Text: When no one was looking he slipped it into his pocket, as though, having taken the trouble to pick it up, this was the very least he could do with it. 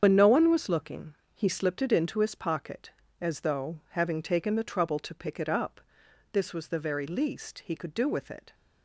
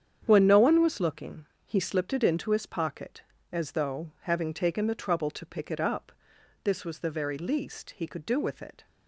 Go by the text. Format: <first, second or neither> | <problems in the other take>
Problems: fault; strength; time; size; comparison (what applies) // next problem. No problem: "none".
second | loses the start of "When"; at 0.0 s; 120 ms // starts louder than the rest; strong; until 1.0 s; 7.5 dB; strong in the second // pauses between "looking" and "he"; slight; at 1.1 s; 0.18 s long; slight in the second